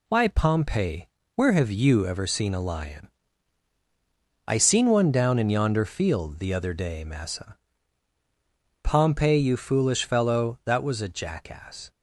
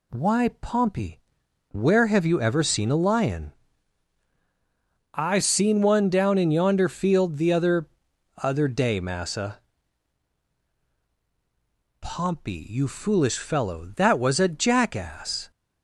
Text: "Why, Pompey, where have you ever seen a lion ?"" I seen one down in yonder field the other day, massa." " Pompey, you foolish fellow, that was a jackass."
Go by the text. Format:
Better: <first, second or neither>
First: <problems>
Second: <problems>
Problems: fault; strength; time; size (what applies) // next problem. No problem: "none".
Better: first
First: none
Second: says "other" twice; at 8.3 s